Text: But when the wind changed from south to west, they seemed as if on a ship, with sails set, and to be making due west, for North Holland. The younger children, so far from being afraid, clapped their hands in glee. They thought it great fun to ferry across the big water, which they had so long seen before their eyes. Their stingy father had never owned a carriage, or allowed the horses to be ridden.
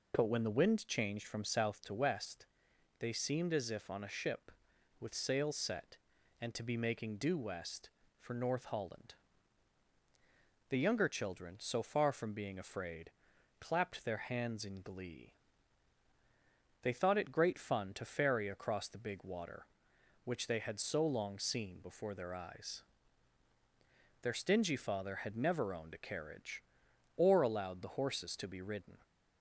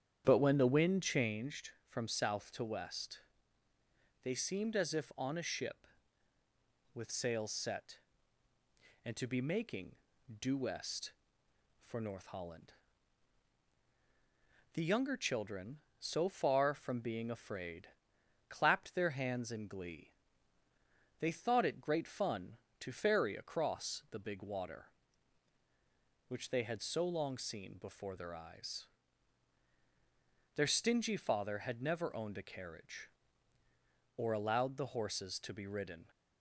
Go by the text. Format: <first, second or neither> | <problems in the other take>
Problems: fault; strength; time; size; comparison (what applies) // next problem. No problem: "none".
first | starts louder than the rest; strong; until 1.4 s; 9 dB // pauses between "making" and "due"; noticeable; at 9.9 s; 0.48 s long